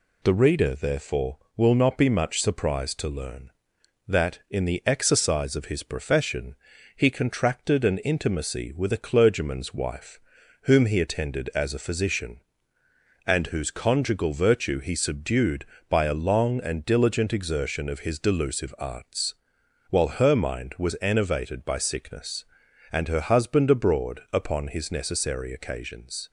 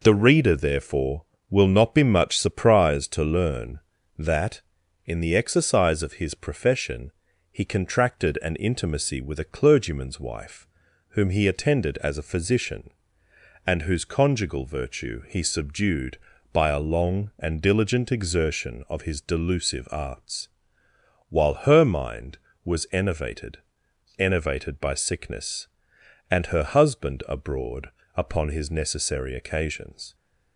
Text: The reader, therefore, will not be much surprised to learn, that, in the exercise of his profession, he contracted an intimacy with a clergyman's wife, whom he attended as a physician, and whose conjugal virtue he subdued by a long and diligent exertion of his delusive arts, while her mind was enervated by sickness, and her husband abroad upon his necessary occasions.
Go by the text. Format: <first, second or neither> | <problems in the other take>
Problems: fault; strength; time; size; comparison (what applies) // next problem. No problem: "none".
first | says "enervated" twice; at 24.1 s // pauses between "abroad" and "upon"; slight; at 27.8 s; 0.26 s long